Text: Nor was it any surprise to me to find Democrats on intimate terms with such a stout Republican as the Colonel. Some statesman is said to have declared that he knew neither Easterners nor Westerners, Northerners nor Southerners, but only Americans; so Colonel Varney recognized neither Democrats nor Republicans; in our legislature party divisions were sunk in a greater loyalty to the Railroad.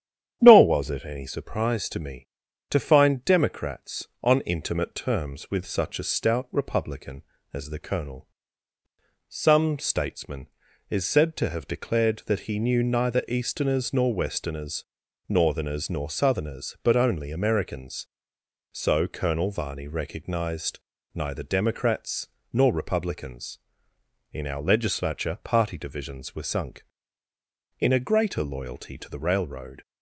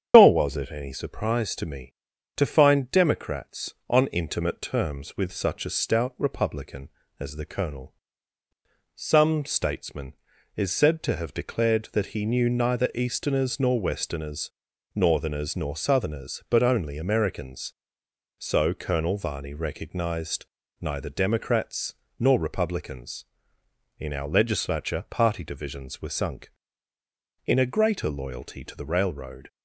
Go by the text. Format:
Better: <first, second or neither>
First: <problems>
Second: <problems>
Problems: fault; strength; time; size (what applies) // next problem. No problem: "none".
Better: first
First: starts louder than the rest; strong; until 1.4 s; 9.5 dB // pauses between "recognized" and "neither"; slight; at 20.7 s; 0.36 s long // pauses between "Democrats" and "nor"; slight; at 22.2 s; 0.22 s long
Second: loses the start of "Nor"; at 0.1 s; 80 ms // starts louder than the rest; strong; until 1.1 s; 8.5 dB // pauses between "recognized" and "neither"; slight; at 20.4 s; 0.36 s long // pauses between "Democrats" and "nor"; slight; at 21.9 s; 0.22 s long